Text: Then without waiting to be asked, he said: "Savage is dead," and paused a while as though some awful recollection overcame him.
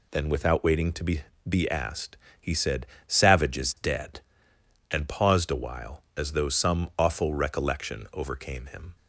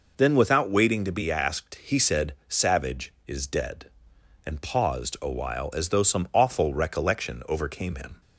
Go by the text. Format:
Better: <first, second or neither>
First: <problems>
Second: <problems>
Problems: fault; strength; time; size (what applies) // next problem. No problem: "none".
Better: second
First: says "be" twice; at 1.4 s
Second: none